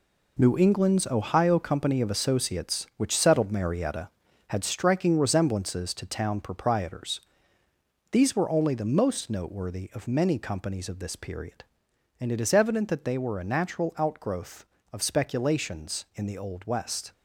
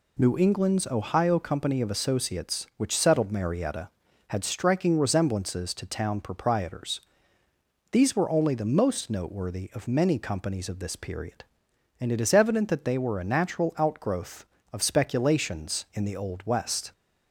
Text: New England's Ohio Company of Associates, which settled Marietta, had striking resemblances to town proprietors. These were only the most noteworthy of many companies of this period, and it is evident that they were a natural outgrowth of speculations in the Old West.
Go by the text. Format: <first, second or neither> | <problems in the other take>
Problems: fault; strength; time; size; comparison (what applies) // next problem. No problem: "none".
second | gets quieter; strong; throughout; 8.5 dB